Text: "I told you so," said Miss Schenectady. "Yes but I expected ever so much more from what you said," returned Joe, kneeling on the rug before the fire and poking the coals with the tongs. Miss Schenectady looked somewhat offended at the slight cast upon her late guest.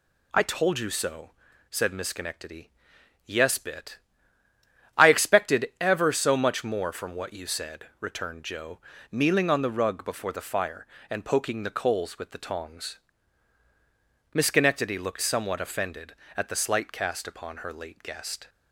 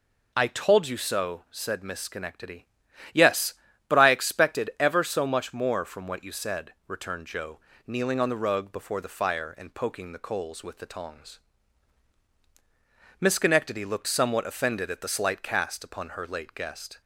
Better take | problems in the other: second | says "bit" for "but"; at 3.5 s

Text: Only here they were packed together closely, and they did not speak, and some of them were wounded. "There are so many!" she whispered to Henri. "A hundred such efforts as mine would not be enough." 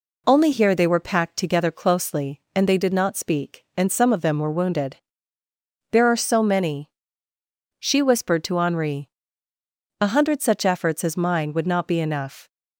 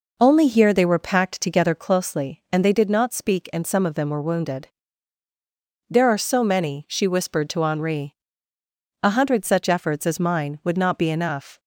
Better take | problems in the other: first | starts louder than the rest; noticeable; until 2.0 s; 5 dB

